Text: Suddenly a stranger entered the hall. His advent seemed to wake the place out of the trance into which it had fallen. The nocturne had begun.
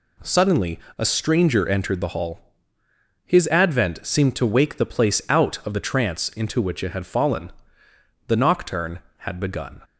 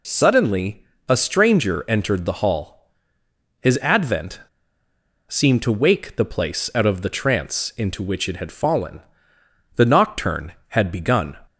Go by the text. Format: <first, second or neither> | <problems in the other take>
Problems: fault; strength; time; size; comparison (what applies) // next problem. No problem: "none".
first | pauses between "Suddenly" and "a"; slight; at 0.8 s; 0.24 s long; slight in the first // pauses between "advent" and "seemed"; noticeable; at 4.3 s; 0.90 s long